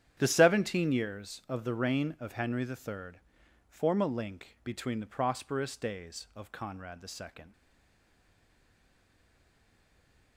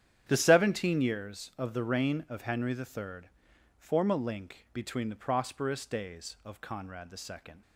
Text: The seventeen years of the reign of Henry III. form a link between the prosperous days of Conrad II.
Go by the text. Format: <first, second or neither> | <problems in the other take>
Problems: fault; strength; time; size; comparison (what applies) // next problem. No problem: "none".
second | starts louder than the rest; strong; until 1.1 s; 9.5 dB; strong in the second // stays silent after the last word; strong; from 7.5 s on; 2.8 s long